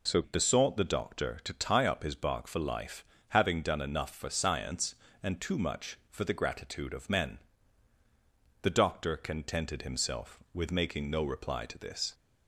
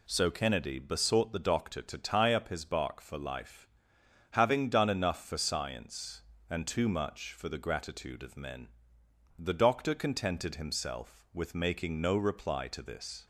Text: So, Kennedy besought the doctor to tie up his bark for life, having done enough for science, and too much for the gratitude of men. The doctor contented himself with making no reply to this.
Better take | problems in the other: second | skips "Kennedy"; at 0.2 s

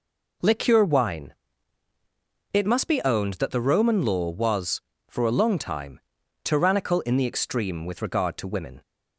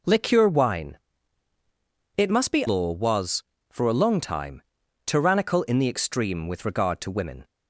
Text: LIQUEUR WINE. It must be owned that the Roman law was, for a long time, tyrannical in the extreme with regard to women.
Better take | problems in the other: first | skips "owned that the Roman"; at 2.6 s

